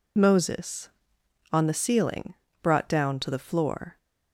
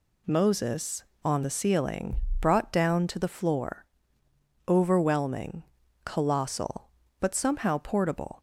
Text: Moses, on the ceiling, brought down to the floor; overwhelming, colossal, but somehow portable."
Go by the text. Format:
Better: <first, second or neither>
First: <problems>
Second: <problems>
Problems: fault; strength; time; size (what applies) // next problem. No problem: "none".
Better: second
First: stops before "overwhelming colossal but somehow portable"; at 3.9 s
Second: none